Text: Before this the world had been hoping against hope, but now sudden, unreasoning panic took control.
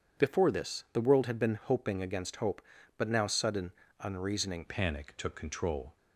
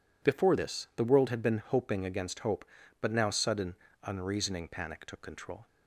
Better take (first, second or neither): second